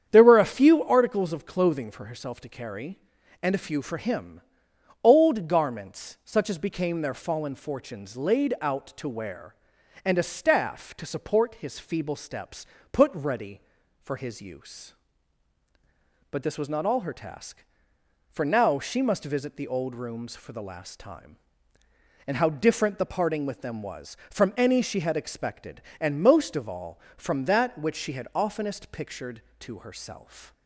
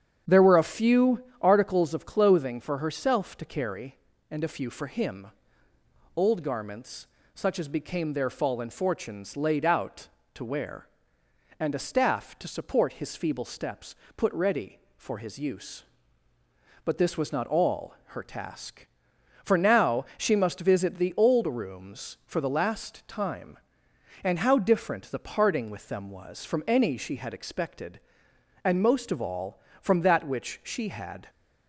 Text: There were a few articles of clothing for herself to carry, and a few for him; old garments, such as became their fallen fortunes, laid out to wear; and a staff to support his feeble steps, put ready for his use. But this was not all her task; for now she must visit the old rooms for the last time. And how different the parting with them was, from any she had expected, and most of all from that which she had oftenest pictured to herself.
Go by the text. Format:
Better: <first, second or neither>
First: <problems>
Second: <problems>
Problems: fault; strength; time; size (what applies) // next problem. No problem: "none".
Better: first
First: starts louder than the rest; strong; until 1.1 s; 8.5 dB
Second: starts louder than the rest; strong; until 1.4 s; 8 dB // pauses between "few" and "articles"; slight; at 1.2 s; 0.16 s long // stops before "oftenest pictured to herself"; at 31.2 s